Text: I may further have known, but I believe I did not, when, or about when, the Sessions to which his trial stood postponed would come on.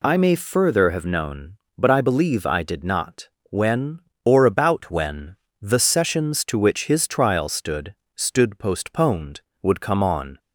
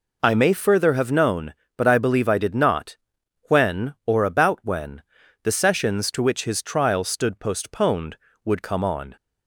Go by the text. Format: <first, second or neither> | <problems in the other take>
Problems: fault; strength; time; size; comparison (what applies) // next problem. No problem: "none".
second | says "stood" twice; at 8.1 s